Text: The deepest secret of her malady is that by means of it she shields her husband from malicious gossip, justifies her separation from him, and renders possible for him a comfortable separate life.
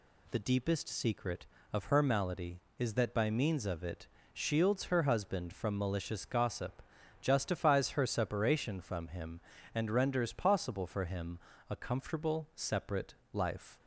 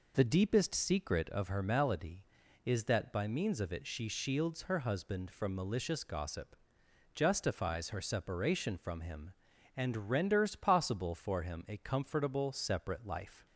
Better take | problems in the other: second | skips "she"; at 4.1 s // pauses between "him" and "a"; slight; at 11.3 s; 0.32 s long // pauses between "separate" and "life"; slight; at 13.1 s; 0.18 s long

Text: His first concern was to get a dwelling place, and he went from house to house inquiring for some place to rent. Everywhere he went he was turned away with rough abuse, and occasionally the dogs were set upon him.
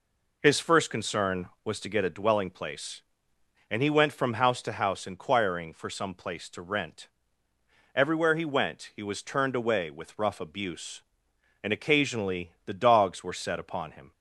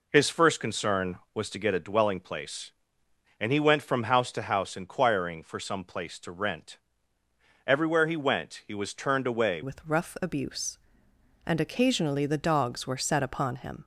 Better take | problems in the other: first | changes voice at "with"; from 9.6 s on; 4.2 s long

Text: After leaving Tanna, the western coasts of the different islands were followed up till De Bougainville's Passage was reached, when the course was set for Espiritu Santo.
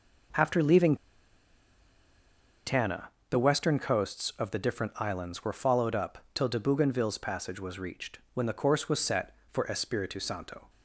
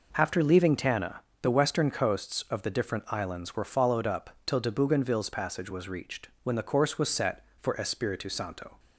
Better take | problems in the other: second | pauses between "leaving" and "Tanna"; strong; at 0.9 s; 1.7 s long

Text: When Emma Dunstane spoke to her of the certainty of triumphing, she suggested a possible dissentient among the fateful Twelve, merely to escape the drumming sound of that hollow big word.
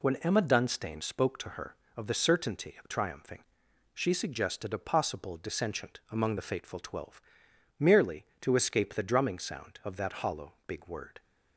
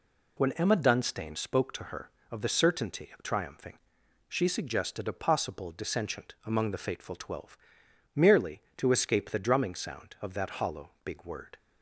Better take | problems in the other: neither | none

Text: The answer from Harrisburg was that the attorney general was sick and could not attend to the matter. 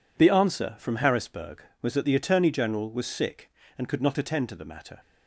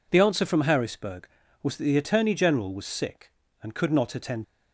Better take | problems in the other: first | stops before "to the matter"; at 4.4 s

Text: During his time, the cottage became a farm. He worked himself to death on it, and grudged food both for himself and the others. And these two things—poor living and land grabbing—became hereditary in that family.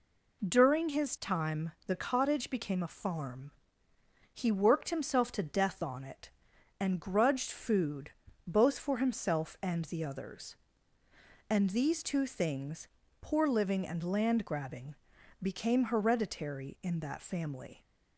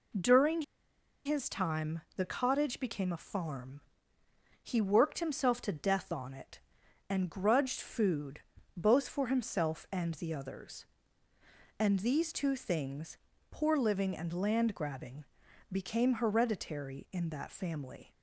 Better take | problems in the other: first | pauses between "During" and "his"; noticeable; at 0.6 s; 0.63 s long // pauses between "food" and "both"; at 8.3 s; 0.38 s long; also in the first

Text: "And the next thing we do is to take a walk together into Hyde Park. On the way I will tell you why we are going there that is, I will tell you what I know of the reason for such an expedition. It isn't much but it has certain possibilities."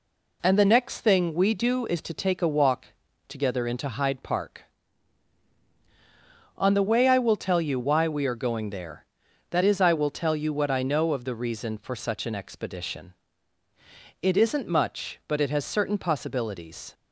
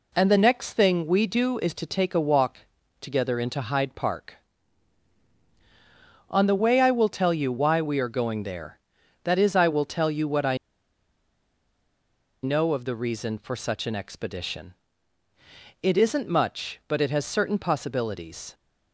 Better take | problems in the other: first | pauses between "walk" and "together"; at 2.5 s; 0.42 s long; also in the first // pauses between "I" and "know"; strong; at 10.5 s; 1.8 s long

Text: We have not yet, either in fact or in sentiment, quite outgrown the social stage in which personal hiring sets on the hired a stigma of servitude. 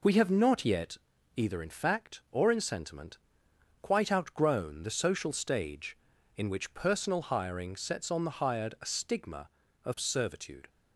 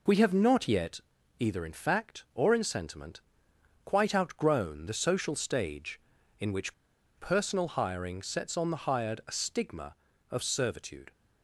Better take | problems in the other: first | pauses between "which" and "personal"; at 6.7 s; 0.45 s long

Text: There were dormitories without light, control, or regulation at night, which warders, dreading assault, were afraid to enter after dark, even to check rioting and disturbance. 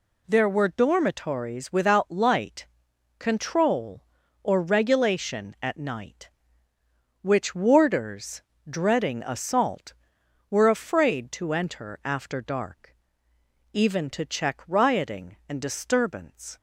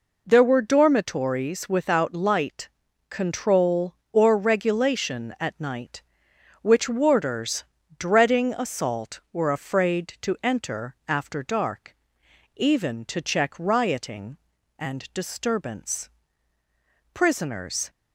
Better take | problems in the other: first | goes on to say "Prisoners"; noticeable; from 17.1 s on; 0.78 s long

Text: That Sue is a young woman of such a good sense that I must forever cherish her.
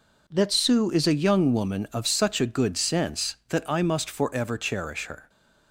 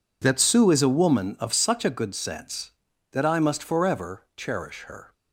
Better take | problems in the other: first | skips "young"; at 0.9 s

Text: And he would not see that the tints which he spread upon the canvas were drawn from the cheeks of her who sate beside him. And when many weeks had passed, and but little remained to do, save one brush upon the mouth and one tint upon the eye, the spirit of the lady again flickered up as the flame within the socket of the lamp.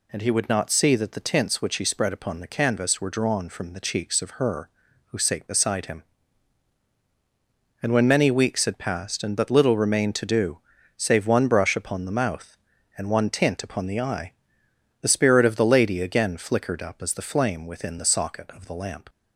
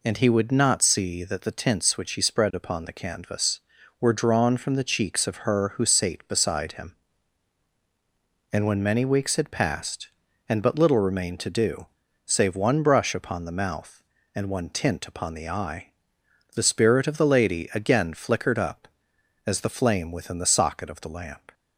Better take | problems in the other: neither | none

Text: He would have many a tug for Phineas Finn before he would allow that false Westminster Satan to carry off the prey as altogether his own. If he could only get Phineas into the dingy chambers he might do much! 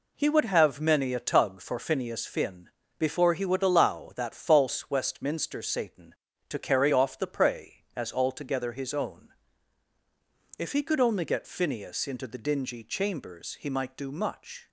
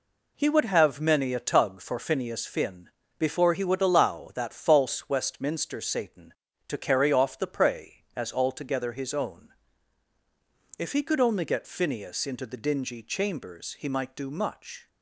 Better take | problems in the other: neither | pauses between "Finn" and "before"; slight; the same in both

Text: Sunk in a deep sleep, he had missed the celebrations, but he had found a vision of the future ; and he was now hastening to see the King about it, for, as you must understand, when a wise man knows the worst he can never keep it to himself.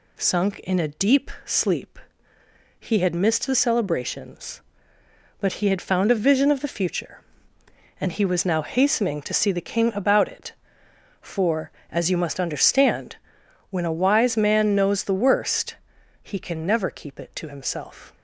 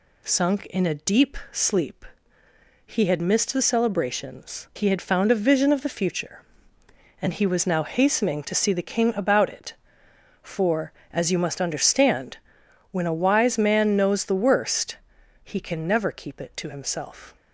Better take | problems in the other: first | pauses between "deep" and "sleep"; slight; at 1.3 s; 0.16 s long; slight in the first // skips "but"; at 4.7 s // pauses between "worst" and "he"; noticeable; at 14.9 s; 0.46 s long; noticeable in the first

